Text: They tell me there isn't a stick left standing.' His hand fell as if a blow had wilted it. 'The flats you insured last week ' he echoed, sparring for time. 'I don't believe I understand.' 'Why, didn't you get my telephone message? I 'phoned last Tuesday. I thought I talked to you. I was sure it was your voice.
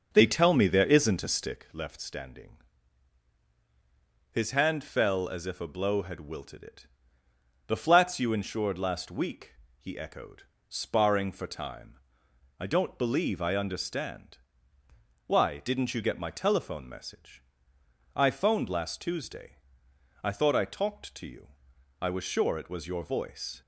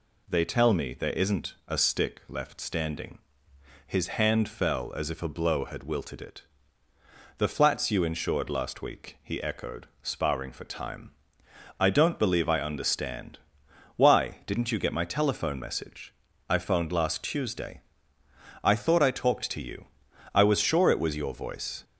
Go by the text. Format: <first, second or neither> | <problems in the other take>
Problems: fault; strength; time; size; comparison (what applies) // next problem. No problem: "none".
second | starts louder than the rest; until 1.6 s; 6 dB